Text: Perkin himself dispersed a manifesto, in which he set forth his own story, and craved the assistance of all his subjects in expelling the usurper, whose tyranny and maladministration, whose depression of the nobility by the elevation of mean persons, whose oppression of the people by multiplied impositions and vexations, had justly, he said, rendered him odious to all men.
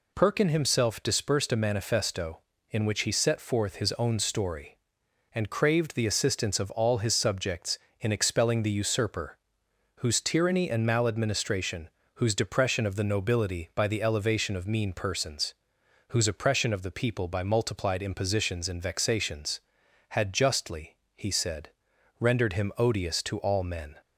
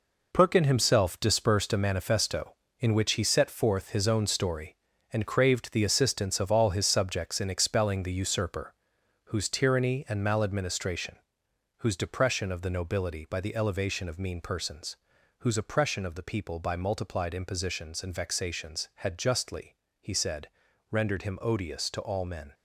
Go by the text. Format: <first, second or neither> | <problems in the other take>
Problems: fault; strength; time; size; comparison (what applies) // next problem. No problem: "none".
first | gets quieter; strong; throughout; 9 dB